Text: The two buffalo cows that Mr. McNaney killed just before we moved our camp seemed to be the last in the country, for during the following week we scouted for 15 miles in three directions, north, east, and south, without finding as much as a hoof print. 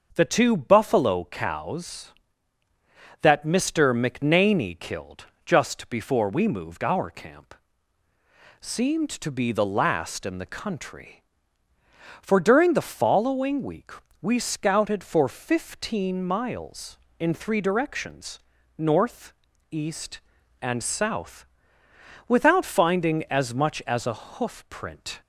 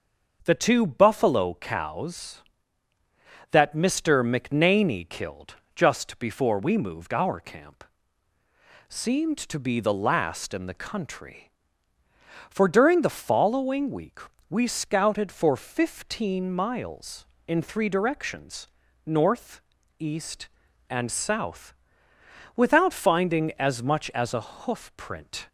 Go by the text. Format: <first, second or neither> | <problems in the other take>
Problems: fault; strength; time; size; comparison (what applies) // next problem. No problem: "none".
neither | starts louder than the rest; the same in both // pauses between "killed" and "just"; slight; the same in both // pauses between "camp" and "seemed"; the same in both // pauses between "week" and "we"; slight; the same in both